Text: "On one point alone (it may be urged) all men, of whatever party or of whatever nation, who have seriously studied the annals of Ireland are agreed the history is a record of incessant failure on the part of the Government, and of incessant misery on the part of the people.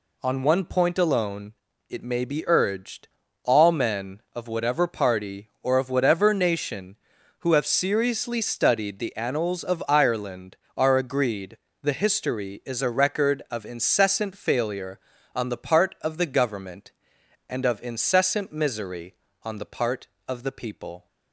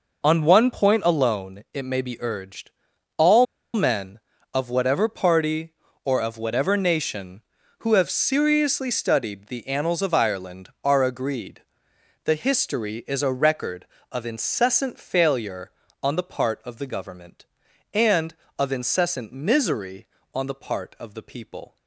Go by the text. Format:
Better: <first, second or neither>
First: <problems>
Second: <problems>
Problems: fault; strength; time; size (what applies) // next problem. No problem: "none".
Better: first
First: pauses between "agreed" and "the"; slight; at 11.5 s; 0.26 s long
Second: pauses between "all" and "men"; slight; at 3.4 s; 0.30 s long // pauses between "agreed" and "the"; noticeable; at 11.6 s; 0.62 s long